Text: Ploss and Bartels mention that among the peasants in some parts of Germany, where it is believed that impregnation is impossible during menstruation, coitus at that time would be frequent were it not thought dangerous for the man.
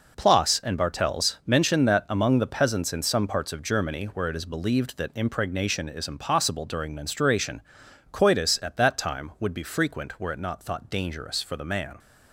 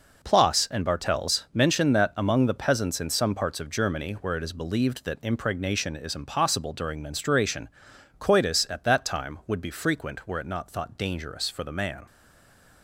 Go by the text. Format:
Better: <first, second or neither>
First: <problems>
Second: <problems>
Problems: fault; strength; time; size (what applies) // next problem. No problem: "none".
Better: first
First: none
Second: stays silent after the last word; slight; from 12.0 s on; 0.8 s long